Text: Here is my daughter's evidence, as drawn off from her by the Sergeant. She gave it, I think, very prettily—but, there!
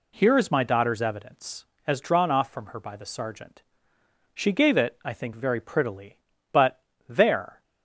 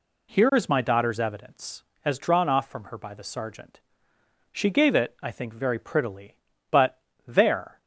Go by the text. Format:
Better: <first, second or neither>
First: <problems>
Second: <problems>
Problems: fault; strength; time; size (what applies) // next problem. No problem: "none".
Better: neither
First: none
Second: none